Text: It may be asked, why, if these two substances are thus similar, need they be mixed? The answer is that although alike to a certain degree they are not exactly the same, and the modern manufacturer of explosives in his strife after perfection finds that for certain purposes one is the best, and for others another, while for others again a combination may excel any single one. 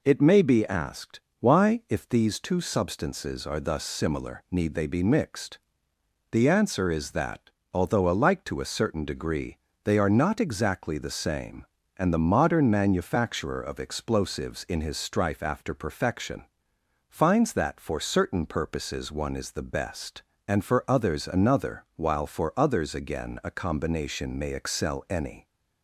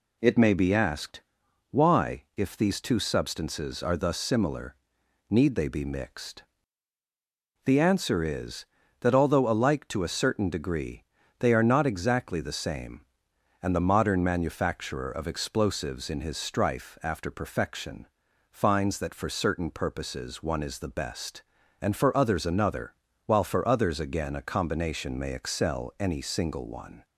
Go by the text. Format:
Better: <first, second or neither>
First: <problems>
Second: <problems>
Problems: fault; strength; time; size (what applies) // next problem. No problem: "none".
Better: second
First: pauses between "that" and "although"; slight; at 7.4 s; 0.24 s long // pauses between "degree" and "they"; slight; at 9.5 s; 0.28 s long // pauses between "perfection" and "finds"; noticeable; at 16.4 s; 0.62 s long // stops before "single one"; at 25.4 s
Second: pauses between "degree" and "they"; slight; at 11.0 s; 0.34 s long // pauses between "perfection" and "finds"; at 18.0 s; 0.44 s long